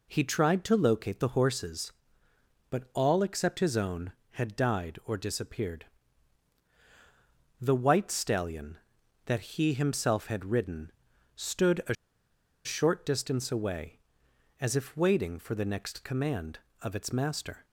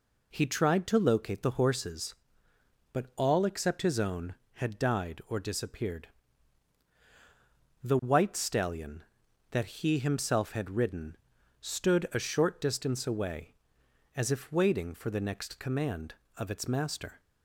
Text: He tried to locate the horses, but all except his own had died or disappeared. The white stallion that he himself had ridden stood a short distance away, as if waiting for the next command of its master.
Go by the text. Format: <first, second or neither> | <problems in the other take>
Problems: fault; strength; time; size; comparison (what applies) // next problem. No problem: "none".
second | pauses between "ridden" and "stood"; noticeable; at 10.9 s; 0.46 s long; noticeable in the second // pauses between "a" and "short"; noticeable; at 11.9 s; 0.70 s long